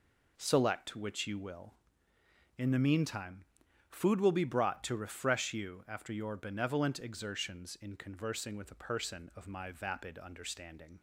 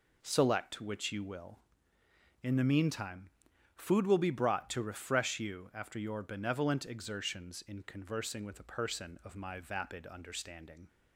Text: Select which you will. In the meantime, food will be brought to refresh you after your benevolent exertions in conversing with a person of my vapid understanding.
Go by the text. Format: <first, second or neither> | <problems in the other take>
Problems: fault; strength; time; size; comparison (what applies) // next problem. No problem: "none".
neither | none